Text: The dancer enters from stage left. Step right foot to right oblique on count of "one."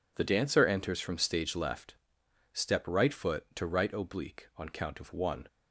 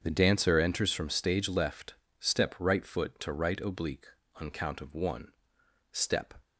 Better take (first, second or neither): first